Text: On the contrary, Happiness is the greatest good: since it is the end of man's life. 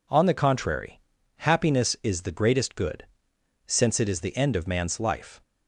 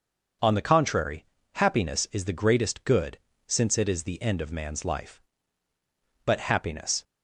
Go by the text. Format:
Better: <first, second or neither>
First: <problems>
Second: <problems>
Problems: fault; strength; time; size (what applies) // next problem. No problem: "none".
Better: first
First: none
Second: starts louder than the rest; until 1.7 s; 6.5 dB // goes on to say "But Happiness"; noticeable; from 6.2 s on; 0.78 s long